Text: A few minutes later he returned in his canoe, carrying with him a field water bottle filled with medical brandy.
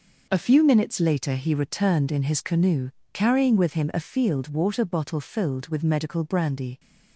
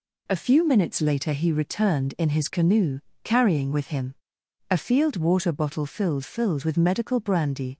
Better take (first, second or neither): first